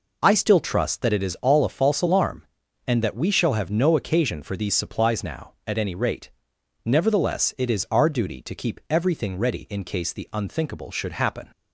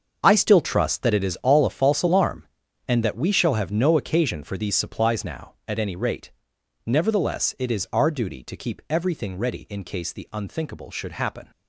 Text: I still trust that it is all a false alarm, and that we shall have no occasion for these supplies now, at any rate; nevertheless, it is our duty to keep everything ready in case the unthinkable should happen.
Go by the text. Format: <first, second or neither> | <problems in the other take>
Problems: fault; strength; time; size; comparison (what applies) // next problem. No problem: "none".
first | gets quieter; strong; throughout; 12 dB